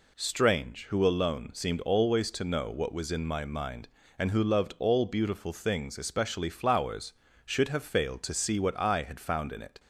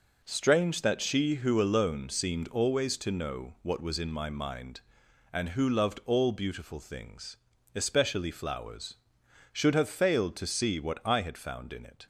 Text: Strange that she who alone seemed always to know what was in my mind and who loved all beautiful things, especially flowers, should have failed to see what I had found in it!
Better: second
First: skips "that she"; at 0.8 s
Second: none

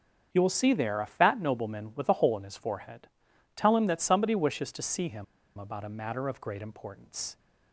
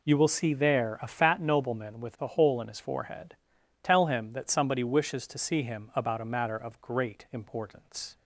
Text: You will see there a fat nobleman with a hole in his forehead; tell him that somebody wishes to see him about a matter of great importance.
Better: second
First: starts louder than the rest; strong; until 1.3 s; 7.5 dB // pauses between "him" and "about"; slight; at 5.2 s; 0.32 s long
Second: none

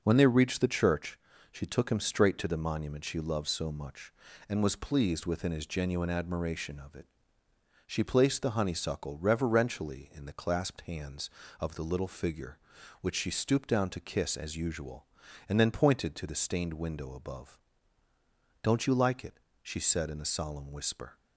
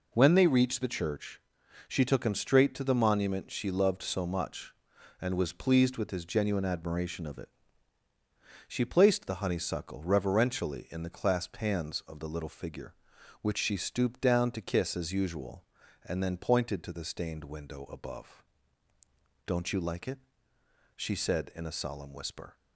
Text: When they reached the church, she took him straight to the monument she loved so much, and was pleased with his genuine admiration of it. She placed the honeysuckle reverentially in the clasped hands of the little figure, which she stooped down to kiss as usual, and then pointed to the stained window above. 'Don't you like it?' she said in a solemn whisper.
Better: second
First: says "within" for "with"; at 5.2 s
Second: none

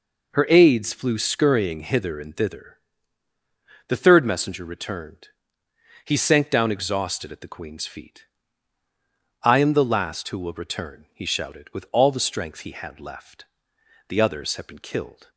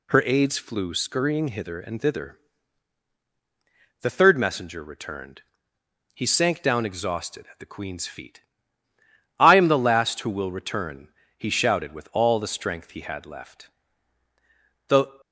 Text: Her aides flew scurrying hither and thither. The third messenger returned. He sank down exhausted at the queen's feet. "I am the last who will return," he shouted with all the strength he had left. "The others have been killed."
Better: first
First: none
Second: stops before "others have been killed"; at 15.2 s

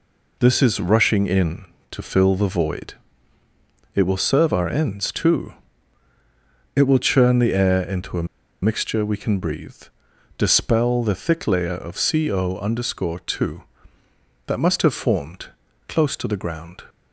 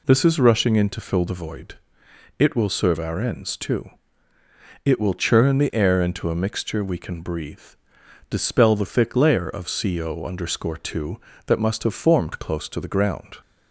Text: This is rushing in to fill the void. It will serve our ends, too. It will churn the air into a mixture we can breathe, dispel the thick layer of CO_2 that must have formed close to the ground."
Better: second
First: pauses between "a" and "mixture"; at 8.2 s; 0.37 s long // pauses between "formed" and "close"; at 15.4 s; 0.42 s long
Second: none

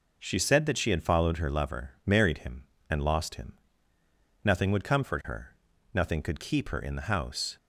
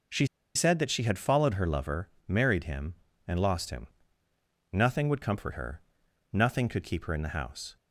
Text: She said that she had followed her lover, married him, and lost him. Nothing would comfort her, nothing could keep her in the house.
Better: first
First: none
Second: pauses between "She" and "said"; slight; at 0.2 s; 0.29 s long

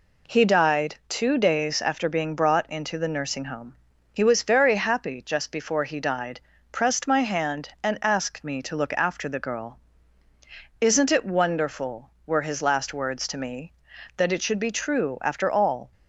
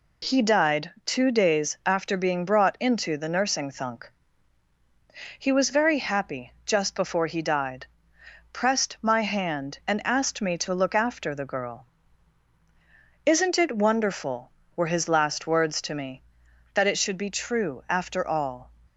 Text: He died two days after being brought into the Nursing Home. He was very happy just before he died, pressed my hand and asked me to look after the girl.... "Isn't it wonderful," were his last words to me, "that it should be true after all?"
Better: first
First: none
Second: says "Thunk" for "Home"; at 3.7 s

